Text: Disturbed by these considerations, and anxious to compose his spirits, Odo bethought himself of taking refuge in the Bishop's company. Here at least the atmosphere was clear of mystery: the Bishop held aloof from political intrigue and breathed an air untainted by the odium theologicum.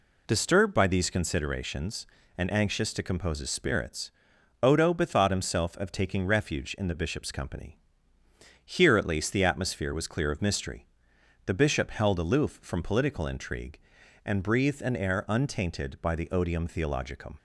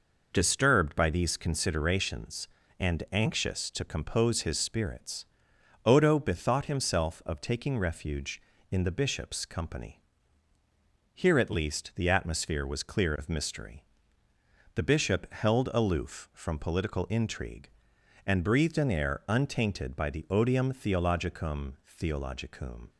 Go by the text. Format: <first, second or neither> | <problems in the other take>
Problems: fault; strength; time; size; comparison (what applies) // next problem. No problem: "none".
first | says "theologicum" twice; at 21.8 s